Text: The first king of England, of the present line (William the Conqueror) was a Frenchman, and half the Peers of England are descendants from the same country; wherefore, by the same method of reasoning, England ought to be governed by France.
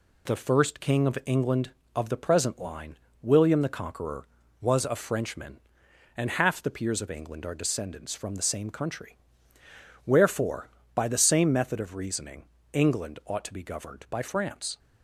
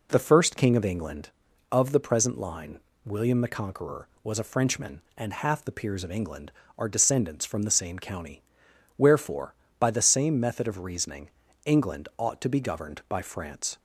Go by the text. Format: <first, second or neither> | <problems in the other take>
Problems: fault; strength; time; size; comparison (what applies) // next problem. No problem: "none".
first | says "county" for "country"; at 7.9 s